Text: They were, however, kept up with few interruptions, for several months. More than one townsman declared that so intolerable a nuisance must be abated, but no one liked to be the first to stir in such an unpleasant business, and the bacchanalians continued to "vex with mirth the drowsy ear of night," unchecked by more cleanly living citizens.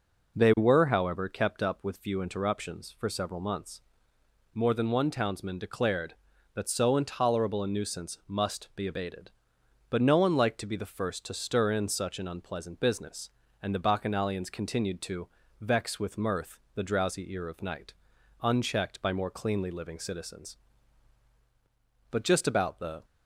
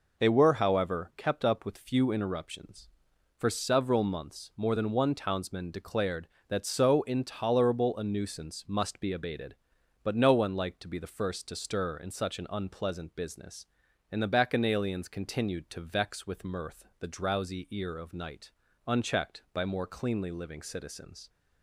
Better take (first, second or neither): second